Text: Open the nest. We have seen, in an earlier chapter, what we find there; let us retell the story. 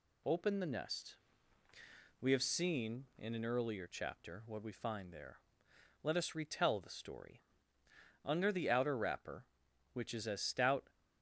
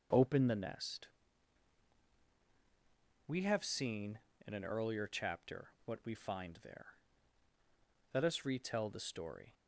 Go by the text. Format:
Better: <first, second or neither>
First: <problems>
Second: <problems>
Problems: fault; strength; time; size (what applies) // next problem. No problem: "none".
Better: second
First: goes on to say "Under the outer wrapper which is as stout"; strong; from 8.2 s on; 2.6 s long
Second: none